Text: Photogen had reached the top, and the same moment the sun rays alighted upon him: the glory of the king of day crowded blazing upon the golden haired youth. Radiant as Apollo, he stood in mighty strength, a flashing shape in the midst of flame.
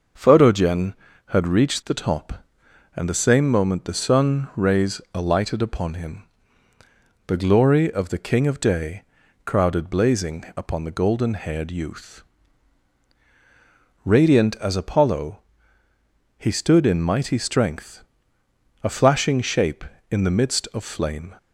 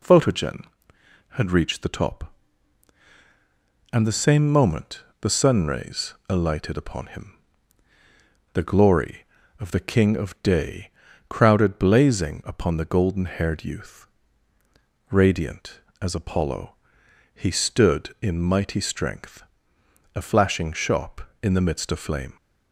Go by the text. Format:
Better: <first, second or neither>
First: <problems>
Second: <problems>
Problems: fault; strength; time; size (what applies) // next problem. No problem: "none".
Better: first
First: pauses between "day" and "crowded"; at 9.0 s; 0.42 s long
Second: pauses between "moment" and "the"; slight; at 5.0 s; 0.20 s long // pauses between "rays" and "alighted"; slight; at 6.1 s; 0.16 s long // pauses between "day" and "crowded"; at 10.9 s; 0.38 s long // says "shop" for "shape"; at 20.7 s